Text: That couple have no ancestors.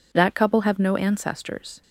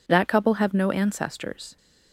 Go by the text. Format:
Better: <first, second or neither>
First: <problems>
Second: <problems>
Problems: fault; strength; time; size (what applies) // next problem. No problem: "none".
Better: neither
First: none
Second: none